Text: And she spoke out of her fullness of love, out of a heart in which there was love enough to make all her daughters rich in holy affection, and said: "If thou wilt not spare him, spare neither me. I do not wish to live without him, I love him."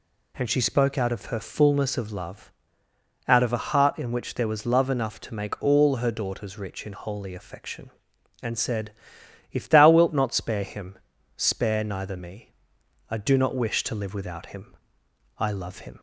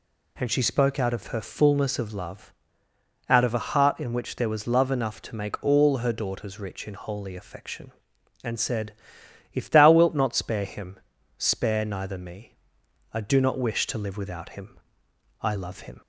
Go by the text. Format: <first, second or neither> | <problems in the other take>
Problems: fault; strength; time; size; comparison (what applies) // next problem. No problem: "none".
neither | none